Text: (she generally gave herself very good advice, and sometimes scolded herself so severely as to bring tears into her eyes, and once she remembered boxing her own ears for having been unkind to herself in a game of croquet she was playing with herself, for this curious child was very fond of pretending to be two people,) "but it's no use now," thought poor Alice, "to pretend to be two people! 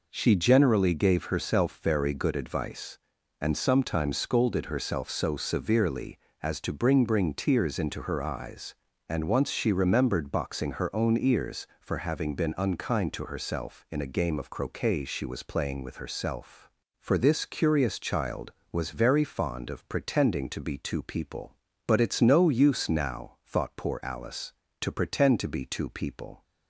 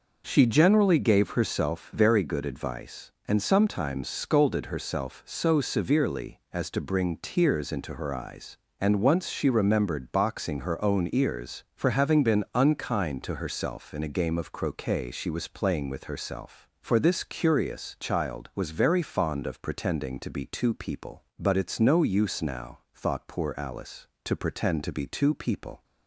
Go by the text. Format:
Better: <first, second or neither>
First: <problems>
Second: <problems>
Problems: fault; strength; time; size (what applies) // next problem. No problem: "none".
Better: second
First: says "bring" twice; at 7.0 s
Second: none